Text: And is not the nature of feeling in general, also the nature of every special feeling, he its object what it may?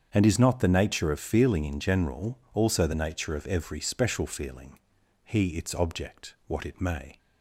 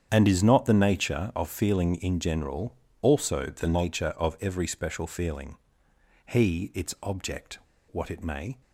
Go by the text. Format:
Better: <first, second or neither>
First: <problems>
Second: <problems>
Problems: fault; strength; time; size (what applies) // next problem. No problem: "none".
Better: first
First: starts louder than the rest; strong; until 1.1 s; 7.5 dB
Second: starts louder than the rest; strong; until 1.1 s; 8.5 dB // pauses between "object" and "what"; slight; at 7.5 s; 0.31 s long